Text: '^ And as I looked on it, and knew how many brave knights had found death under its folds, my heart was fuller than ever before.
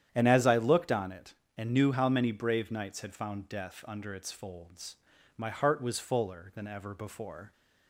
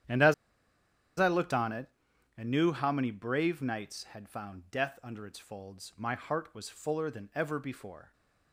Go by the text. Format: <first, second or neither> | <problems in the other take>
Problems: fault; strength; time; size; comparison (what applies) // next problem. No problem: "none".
first | starts louder than the rest; strong; until 2.4 s; 10 dB; strong in the first // pauses between "as" and "I"; noticeable; at 0.3 s; 0.85 s long